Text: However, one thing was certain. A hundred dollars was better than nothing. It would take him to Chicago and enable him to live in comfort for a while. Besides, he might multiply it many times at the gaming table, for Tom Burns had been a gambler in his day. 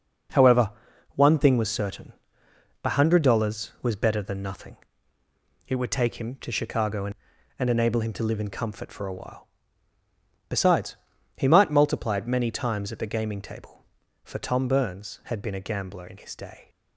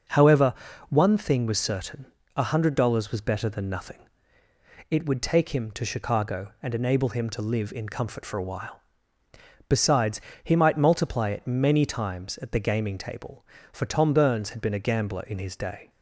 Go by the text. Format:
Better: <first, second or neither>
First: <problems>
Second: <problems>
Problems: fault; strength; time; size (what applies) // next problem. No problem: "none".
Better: second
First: says "and" twice; at 7.5 s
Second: none